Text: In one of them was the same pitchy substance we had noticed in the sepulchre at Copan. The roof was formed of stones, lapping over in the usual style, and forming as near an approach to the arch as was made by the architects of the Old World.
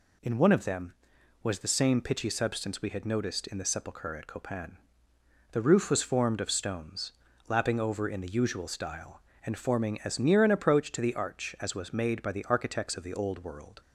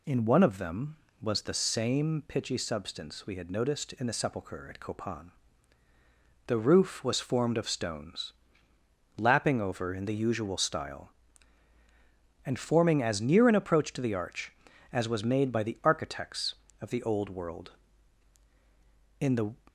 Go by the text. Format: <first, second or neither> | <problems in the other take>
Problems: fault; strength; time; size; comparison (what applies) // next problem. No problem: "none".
first | goes on to say "In the"; slight; from 19.2 s on; 0.34 s long